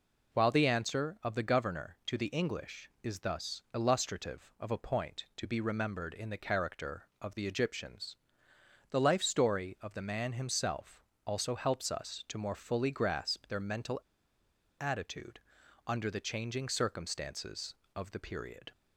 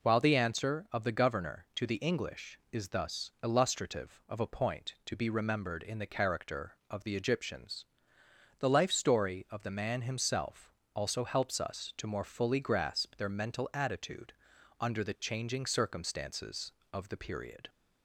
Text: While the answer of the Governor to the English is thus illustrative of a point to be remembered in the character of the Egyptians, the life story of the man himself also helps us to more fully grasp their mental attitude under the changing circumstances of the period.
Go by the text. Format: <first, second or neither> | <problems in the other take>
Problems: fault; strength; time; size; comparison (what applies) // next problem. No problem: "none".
second | pauses between "himself" and "also"; slight; at 11.0 s; 0.22 s long; slight in the second // pauses between "mental" and "attitude"; noticeable; at 13.9 s; 0.81 s long // pauses between "attitude" and "under"; noticeable; at 15.3 s; 0.46 s long; noticeable in the second